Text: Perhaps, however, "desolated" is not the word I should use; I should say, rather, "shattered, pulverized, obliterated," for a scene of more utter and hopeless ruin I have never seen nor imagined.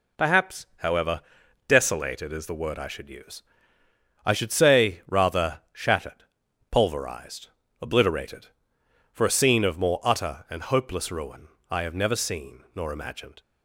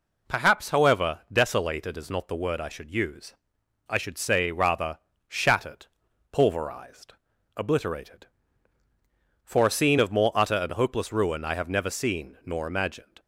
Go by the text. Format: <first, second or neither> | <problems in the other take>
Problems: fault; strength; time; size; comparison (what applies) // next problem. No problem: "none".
second | skips "not"; at 2.4 s // pauses between "ruin" and "I"; slight; at 11.4 s; 0.22 s long